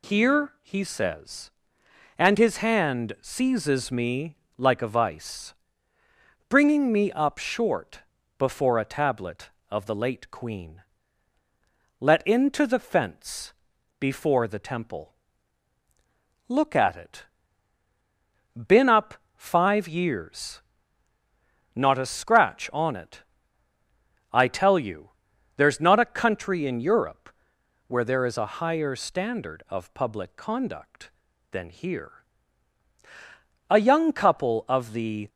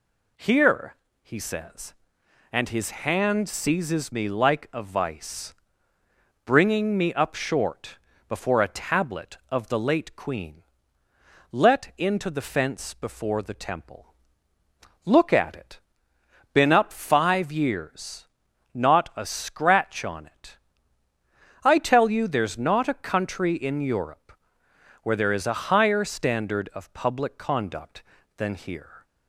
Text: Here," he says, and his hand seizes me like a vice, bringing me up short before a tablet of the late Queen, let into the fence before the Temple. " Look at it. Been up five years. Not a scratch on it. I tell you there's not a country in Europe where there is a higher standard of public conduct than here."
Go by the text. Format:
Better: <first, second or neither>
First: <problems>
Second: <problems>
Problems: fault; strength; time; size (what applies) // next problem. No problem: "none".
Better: second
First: pauses between "me" and "like"; slight; at 4.3 s; 0.22 s long // pauses between "short" and "before"; slight; at 8.0 s; 0.36 s long // pauses between "fence" and "before"; at 13.5 s; 0.44 s long // pauses between "up" and "five"; slight; at 19.1 s; 0.20 s long // pauses between "you" and "there's"; noticeable; at 25.0 s; 0.48 s long // pauses between "Europe" and "where"; noticeable; at 27.2 s; 0.64 s long // goes on to say "A young couple of the"; from 33.6 s on; 1.6 s long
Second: pauses between "short" and "before"; slight; at 7.9 s; 0.30 s long // pauses between "Europe" and "where"; noticeable; at 24.3 s; 0.68 s long